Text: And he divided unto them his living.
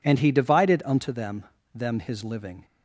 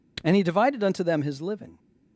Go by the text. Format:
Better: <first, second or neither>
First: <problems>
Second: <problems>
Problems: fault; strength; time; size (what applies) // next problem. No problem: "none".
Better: second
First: says "them" twice; at 1.7 s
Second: none